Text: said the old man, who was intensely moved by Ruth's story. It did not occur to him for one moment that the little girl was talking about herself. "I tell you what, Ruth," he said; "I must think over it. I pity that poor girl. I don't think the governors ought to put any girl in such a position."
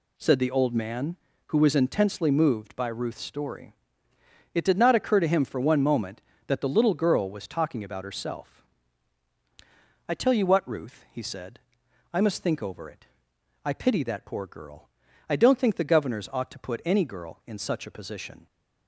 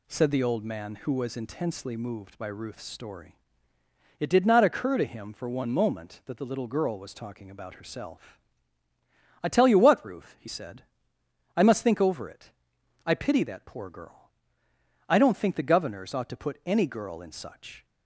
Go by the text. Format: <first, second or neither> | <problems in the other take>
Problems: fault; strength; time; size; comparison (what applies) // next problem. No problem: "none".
first | stops before "a position"; at 17.8 s